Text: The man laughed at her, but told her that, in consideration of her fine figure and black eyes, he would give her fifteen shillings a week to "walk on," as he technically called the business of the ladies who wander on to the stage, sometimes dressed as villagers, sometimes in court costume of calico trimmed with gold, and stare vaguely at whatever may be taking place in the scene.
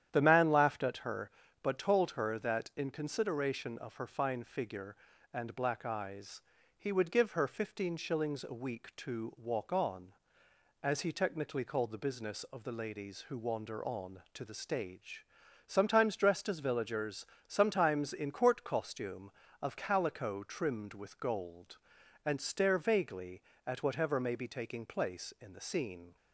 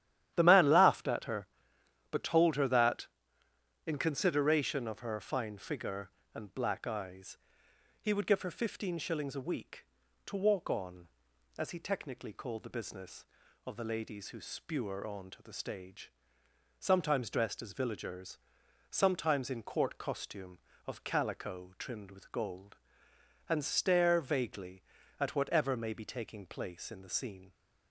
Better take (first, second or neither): first